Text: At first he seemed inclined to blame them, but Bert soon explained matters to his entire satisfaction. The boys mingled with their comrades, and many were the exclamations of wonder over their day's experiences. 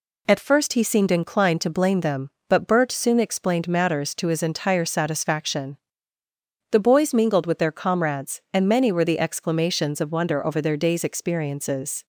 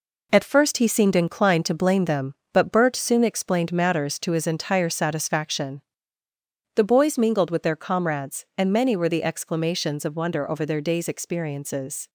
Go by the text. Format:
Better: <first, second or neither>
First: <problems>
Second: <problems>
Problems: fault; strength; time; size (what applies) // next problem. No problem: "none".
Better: first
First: none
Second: gets quieter; throughout; 6.5 dB